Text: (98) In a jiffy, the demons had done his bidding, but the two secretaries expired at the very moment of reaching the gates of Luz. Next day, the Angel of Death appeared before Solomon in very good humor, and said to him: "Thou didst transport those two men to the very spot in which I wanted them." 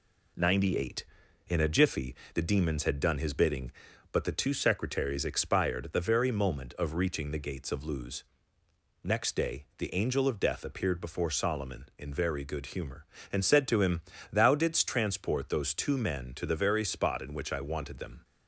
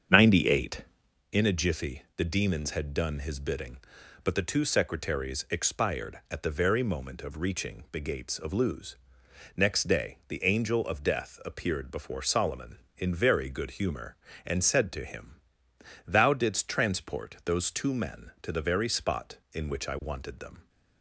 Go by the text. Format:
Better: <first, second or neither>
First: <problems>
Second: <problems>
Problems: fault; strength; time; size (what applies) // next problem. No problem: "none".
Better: first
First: none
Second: starts louder than the rest; strong; until 1.3 s; 7.5 dB